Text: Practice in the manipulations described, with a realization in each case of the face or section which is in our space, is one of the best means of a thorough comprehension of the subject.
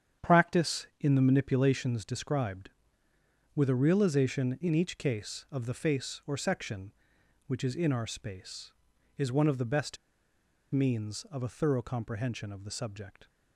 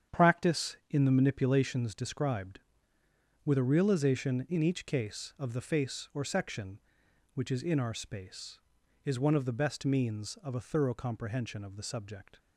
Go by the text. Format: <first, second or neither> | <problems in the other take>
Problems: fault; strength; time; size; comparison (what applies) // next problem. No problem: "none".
second | starts louder than the rest; strong; until 1.3 s; 8.5 dB; strong in the second // pauses between "best" and "means"; noticeable; at 9.9 s; 0.75 s long